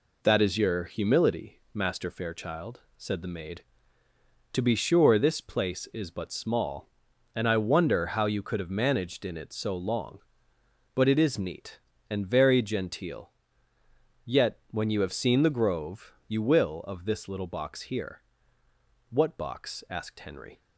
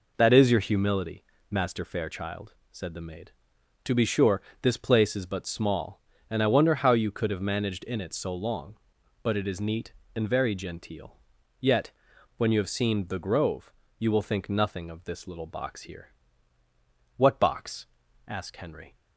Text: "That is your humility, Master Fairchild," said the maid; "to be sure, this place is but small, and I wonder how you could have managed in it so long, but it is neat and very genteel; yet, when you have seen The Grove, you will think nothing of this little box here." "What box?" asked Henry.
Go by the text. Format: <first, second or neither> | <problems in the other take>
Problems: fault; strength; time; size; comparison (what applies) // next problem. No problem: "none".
second | skips "think nothing"; at 16.8 s